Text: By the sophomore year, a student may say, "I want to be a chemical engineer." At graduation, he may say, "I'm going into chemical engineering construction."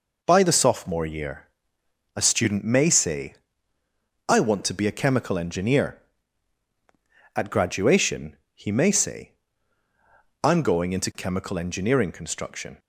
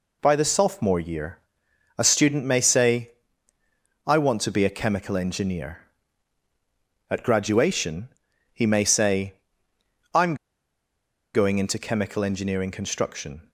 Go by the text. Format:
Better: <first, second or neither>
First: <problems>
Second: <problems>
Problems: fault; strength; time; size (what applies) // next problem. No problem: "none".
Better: first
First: none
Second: pauses between "I'm" and "going"; at 10.3 s; 0.98 s long